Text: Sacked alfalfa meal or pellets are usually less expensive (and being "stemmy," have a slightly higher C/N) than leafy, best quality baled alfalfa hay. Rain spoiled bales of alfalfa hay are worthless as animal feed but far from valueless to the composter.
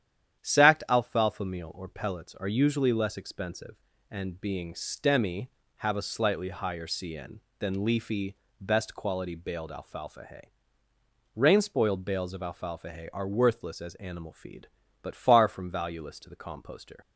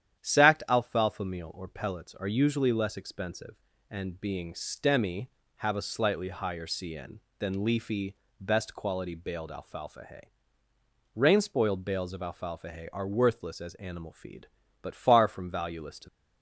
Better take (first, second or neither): first